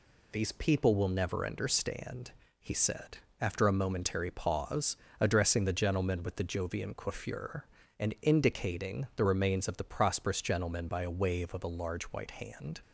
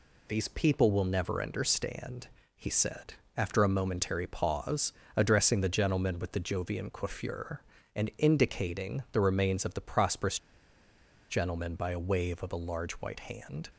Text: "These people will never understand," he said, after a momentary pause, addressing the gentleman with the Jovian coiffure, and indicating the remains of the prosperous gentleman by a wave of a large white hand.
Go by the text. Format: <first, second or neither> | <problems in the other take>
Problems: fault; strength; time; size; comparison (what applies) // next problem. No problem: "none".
first | pauses between "prosperous" and "gentleman"; noticeable; at 10.3 s; 0.91 s long